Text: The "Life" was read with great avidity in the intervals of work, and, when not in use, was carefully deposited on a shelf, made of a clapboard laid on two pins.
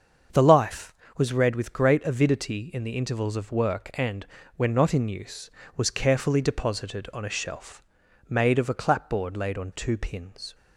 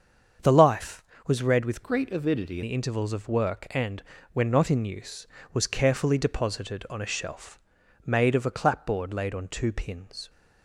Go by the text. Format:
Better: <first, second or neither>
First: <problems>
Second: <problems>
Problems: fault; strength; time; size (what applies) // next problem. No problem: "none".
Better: first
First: starts louder than the rest; until 1.5 s; 6.5 dB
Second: starts louder than the rest; until 1.6 s; 7 dB // changes voice from "great" to "in"; from 1.8 to 2.6 s; 0.8 s long